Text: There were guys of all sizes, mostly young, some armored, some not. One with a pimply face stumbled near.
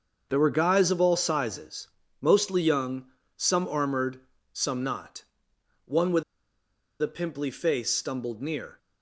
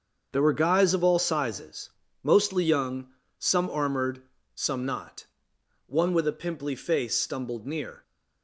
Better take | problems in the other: second | starts louder than the rest; until 1.3 s; 6.5 dB; also in the second // pauses between "with" and "a"; noticeable; at 6.2 s; 0.78 s long

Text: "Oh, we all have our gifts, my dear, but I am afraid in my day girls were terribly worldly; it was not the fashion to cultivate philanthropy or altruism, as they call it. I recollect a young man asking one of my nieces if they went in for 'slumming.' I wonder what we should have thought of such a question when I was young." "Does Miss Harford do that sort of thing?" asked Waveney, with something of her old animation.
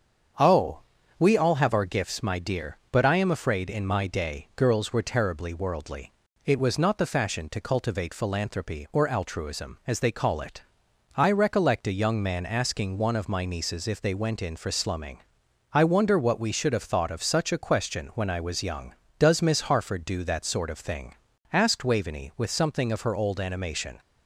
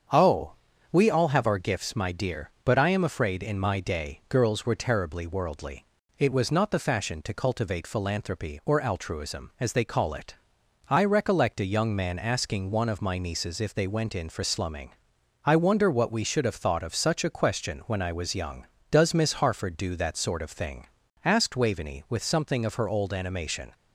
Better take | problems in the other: neither | starts louder than the rest; strong; the same in both

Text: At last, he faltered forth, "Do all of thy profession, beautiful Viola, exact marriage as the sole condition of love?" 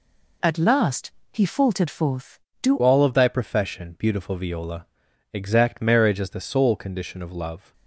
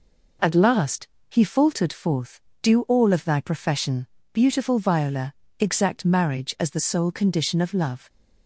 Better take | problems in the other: second | changes voice at "all"; from 2.8 s on; 4.9 s long

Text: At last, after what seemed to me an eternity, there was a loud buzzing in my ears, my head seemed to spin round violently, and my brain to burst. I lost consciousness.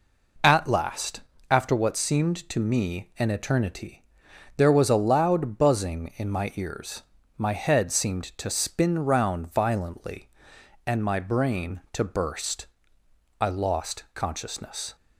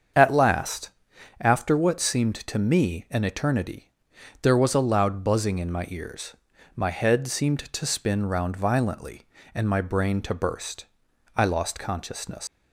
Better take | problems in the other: first | starts louder than the rest; strong; until 1.6 s; 7.5 dB // leaves "consciousness" unfinished; at 12.4 s; 125 ms

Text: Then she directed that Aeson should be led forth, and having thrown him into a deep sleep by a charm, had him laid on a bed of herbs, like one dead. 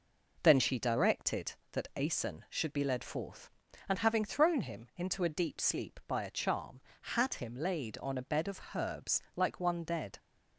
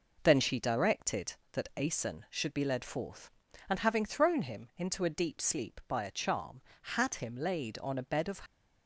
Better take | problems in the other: first | stops before "herbs like one dead"; at 8.4 s

